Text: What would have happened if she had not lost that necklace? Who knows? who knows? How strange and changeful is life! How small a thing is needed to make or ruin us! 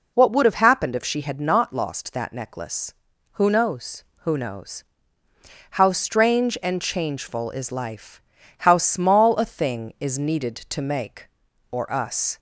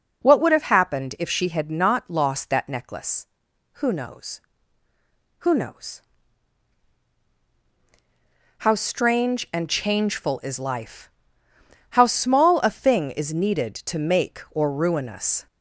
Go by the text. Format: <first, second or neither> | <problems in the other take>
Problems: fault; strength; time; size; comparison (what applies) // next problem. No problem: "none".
second | skips "ruin"; at 11.9 s